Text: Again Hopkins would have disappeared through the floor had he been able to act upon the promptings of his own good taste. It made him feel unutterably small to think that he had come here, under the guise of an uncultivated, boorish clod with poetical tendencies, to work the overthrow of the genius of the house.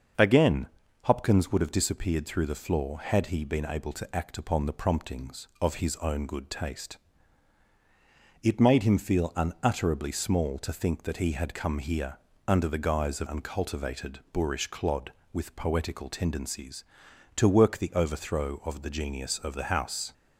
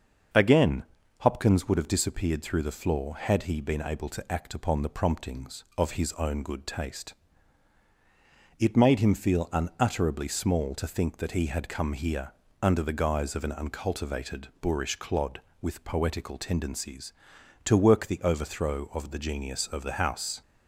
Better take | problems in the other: second | starts louder than the rest; until 1.5 s; 6.5 dB; also in the second // pauses between "Again" and "Hopkins"; slight; at 0.6 s; 0.36 s long; slight in the second // skips "an"; at 13.2 s

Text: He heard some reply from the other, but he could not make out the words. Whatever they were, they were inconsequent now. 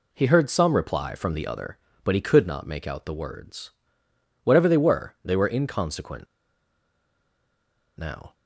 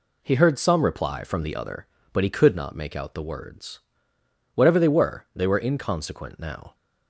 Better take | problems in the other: second | pauses between "inconsequent" and "now"; strong; at 6.2 s; 1.7 s long

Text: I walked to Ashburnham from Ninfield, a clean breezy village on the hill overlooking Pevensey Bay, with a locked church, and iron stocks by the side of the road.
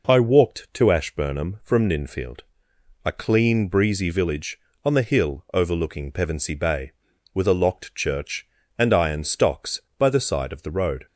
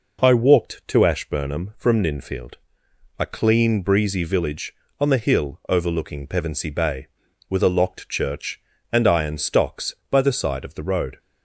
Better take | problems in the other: neither | none

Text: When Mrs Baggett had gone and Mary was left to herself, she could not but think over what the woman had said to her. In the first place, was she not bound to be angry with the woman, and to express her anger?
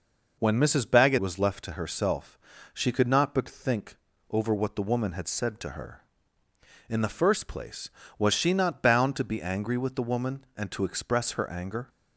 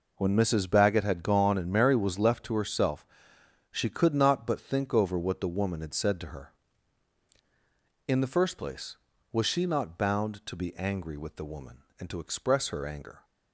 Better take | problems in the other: second | skips "had gone and Mary"; at 1.1 s // pauses between "think" and "over"; slight; at 3.9 s; 0.34 s long

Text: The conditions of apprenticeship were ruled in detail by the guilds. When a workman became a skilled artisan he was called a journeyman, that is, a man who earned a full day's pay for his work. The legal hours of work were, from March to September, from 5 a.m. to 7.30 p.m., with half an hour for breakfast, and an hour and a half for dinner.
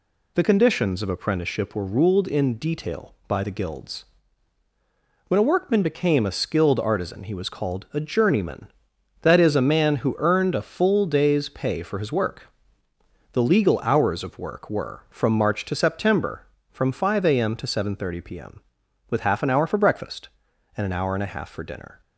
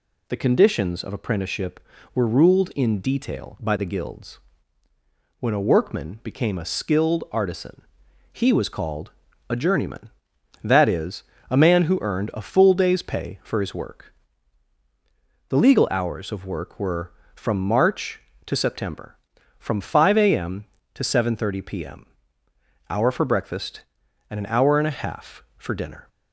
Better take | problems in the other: first | pauses between "artisan" and "he"; noticeable; at 7.8 s; 0.50 s long // pauses between "called" and "a"; slight; at 9.1 s; 0.36 s long // skips "with half an"; at 22.4 s

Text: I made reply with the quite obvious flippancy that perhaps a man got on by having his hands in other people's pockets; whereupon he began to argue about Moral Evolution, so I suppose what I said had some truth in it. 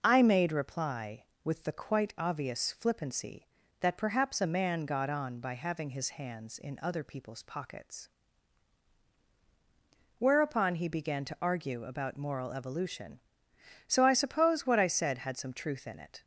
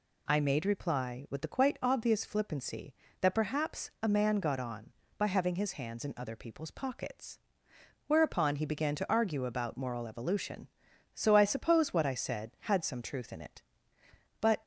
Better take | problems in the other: first | goes on to say "But"; slight; from 14.3 s on; 0.24 s long

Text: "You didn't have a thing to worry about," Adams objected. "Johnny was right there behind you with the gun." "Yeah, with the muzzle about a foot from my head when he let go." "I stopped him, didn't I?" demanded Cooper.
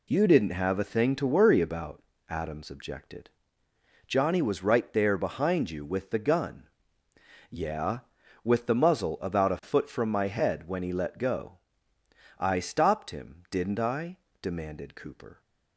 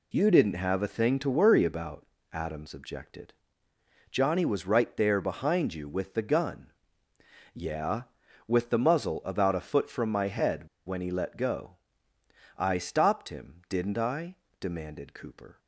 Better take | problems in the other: first | pauses between "head" and "when"; slight; at 10.6 s; 0.19 s long

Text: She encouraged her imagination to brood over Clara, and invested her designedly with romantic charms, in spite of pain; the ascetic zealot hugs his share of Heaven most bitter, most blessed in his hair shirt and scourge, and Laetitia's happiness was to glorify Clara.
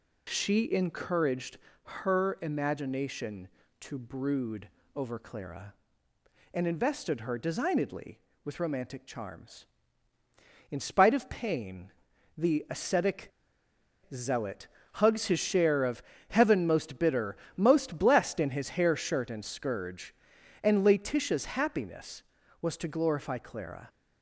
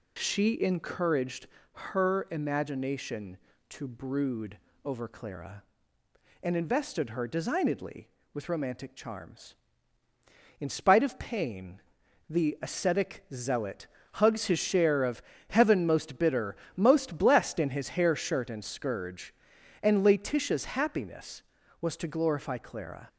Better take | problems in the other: second | pauses between "encouraged" and "her"; slight; at 1.5 s; 0.28 s long; slight in the second // pauses between "brood" and "over"; slight; at 4.6 s; 0.26 s long; slight in the second // pauses between "ascetic" and "zealot"; noticeable; at 13.3 s; 0.82 s long // pauses between "zealot" and "hugs"; slight; at 14.6 s; 0.28 s long; slight in the second // pauses between "of" and "Heaven"; slight; at 16.0 s; 0.26 s long; slight in the second

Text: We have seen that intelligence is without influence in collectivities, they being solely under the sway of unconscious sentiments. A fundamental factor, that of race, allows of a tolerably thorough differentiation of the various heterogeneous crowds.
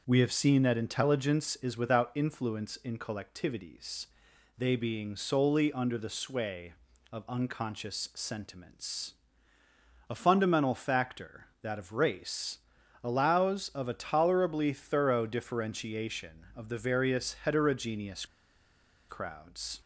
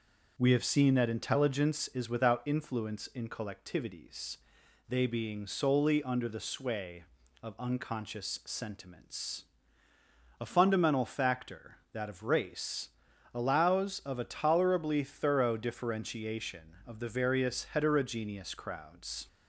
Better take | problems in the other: second | pauses between "heterogeneous" and "crowds"; noticeable; at 18.2 s; 0.82 s long

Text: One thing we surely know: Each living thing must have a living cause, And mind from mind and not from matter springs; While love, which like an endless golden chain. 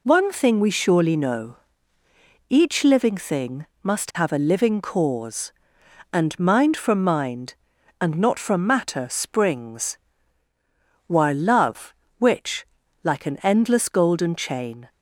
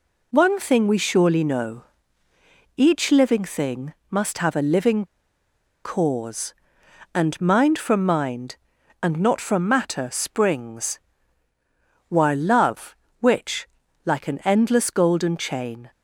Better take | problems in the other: first | pauses between "thing" and "must"; slight; at 3.9 s; 0.16 s long; slight in the first // pauses between "living" and "cause"; noticeable; at 5.0 s; 0.78 s long // pauses between "which" and "like"; slight; at 13.6 s; 0.36 s long; slight in the first

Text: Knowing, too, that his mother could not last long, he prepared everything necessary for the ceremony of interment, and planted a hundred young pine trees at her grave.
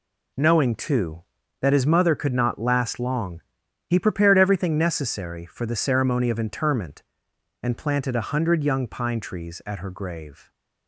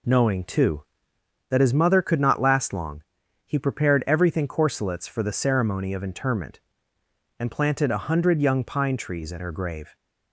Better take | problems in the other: first | says "corselets" for "necessary"; at 4.4 s

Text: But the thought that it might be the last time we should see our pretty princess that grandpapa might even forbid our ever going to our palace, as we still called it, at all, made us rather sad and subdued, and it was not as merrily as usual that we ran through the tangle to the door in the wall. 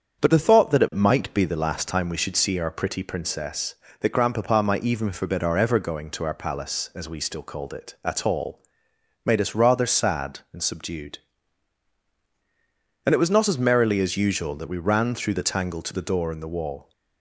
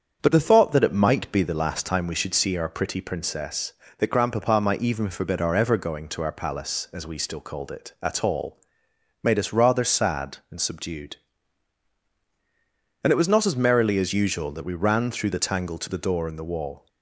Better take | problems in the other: neither | starts louder than the rest; strong; the same in both

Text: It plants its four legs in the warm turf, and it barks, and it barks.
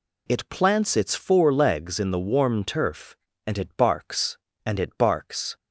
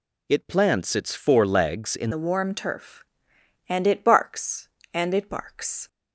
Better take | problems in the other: first | changes voice at "the"; from 2.1 s on; 3.7 s long

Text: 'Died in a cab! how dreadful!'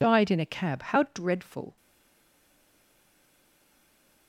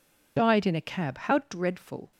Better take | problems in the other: second | stays silent after the last word; strong; from 1.7 s on; 2.5 s long

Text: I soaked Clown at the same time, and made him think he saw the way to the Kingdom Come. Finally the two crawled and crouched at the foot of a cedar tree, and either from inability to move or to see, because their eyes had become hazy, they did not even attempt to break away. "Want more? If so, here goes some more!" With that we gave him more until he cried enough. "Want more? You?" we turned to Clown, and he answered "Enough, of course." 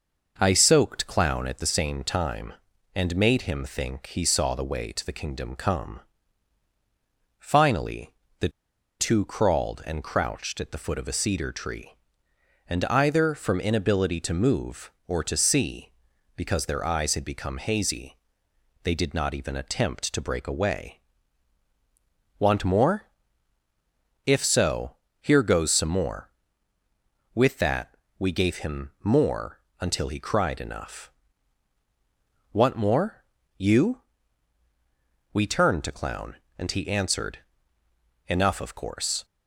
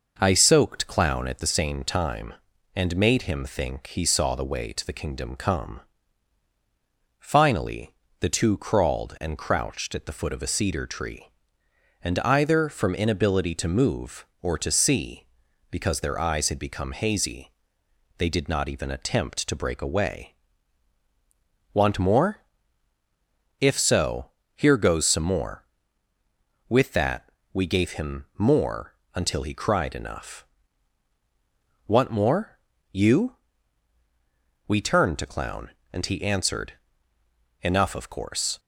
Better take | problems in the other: second | pauses between "Finally" and "the"; slight; at 8.1 s; 0.26 s long; slight in the second // pauses between "the" and "two"; noticeable; at 8.4 s; 0.51 s long // pauses between "that" and "we"; slight; at 27.9 s; 0.22 s long; slight in the second // pauses between "more" and "until"; slight; at 29.5 s; 0.22 s long; slight in the second // pauses between "answered" and "Enough"; noticeable; at 37.3 s; 0.88 s long; noticeable in the second

